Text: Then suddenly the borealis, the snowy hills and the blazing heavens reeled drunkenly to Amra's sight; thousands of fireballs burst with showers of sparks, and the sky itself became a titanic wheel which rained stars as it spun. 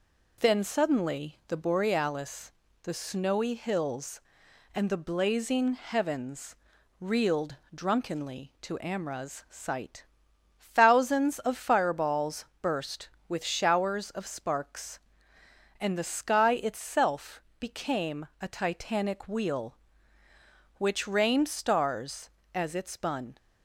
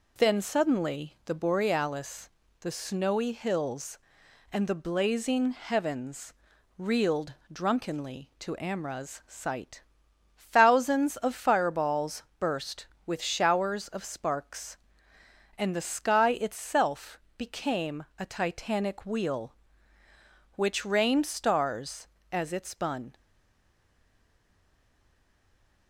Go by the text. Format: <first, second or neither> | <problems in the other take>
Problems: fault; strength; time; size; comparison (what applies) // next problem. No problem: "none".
first | pauses between "heavens" and "reeled"; noticeable; at 6.3 s; 0.46 s long; noticeable in the first // pauses between "reeled" and "drunkenly"; slight; at 7.3 s; 0.20 s long; slight in the first // pauses between "fireballs" and "burst"; slight; at 12.2 s; 0.16 s long; slight in the first // pauses between "itself" and "became"; slight; at 17.1 s; 0.18 s long; slight in the first // stays silent after the last word; strong; from 23.1 s on; 2.7 s long